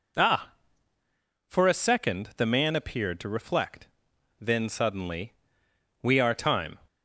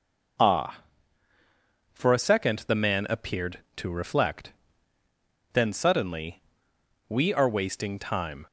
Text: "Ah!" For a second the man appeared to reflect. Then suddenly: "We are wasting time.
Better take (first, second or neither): second